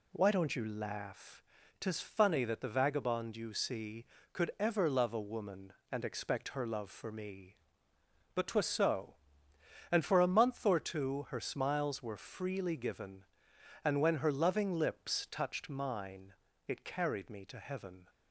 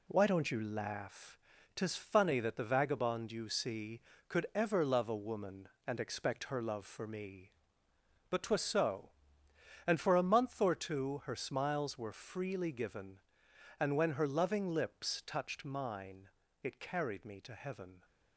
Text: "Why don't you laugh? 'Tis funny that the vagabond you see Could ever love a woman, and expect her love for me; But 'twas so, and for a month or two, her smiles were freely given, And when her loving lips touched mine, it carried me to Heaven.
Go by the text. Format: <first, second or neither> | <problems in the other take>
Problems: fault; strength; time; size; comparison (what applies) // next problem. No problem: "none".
first | gets quieter; throughout; 6.5 dB